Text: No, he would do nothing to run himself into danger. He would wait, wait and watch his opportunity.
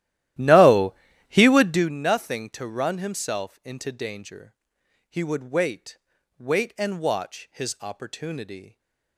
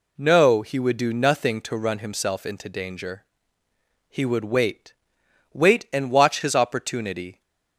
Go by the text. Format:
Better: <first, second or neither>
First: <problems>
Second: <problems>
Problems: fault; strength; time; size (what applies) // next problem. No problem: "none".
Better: second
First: starts louder than the rest; strong; until 2.0 s; 14 dB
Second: none